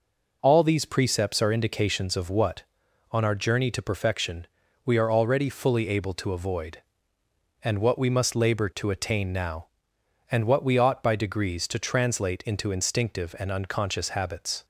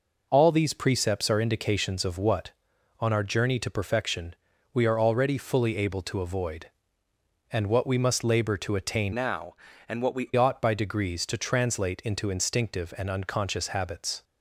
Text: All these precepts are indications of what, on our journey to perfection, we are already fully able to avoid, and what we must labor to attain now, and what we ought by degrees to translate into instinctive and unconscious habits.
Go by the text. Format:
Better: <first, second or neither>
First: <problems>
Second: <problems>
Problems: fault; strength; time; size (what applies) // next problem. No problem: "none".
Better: first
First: none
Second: changes voice from "now" to "we"; from 9.1 to 10.3 s; 1.2 s long